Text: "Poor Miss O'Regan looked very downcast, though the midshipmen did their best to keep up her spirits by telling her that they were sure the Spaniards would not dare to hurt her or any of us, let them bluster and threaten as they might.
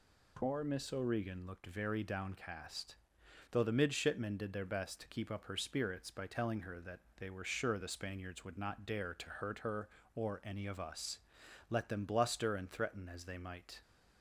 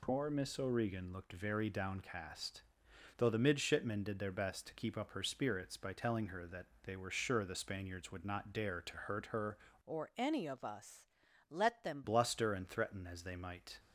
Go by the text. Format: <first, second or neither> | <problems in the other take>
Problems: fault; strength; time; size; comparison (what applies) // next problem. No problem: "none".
first | pauses between "that" and "they"; slight; at 6.6 s; 0.16 s long; slight in the first // changes voice from "or" to "them"; from 9.8 to 12.0 s; 2.2 s long